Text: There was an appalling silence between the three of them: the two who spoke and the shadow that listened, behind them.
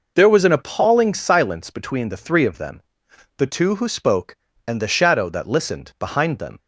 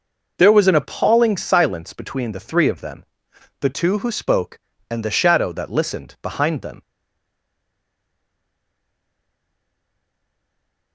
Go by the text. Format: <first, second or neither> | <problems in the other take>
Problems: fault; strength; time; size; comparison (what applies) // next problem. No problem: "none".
first | stays silent after the last word; strong; from 6.8 s on; 4.1 s long